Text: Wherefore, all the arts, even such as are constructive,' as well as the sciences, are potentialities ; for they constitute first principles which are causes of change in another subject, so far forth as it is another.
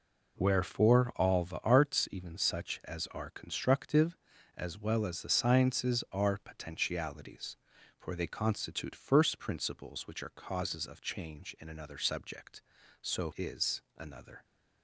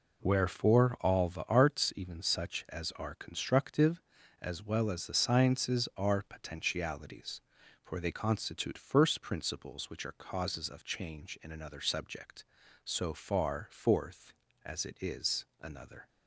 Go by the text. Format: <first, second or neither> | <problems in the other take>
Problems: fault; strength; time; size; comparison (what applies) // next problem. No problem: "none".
second | skips "far forth as it"; at 13.3 s // pauses between "is" and "another"; slight; at 13.7 s; 0.18 s long; slight in the second